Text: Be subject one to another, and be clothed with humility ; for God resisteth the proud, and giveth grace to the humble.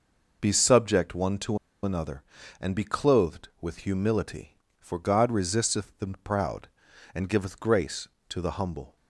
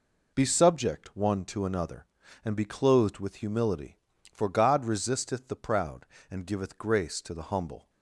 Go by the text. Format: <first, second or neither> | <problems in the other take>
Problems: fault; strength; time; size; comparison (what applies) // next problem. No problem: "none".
second | pauses between "to" and "another"; slight; at 1.5 s; 0.25 s long // pauses between "the" and "proud"; slight; at 6.0 s; 0.16 s long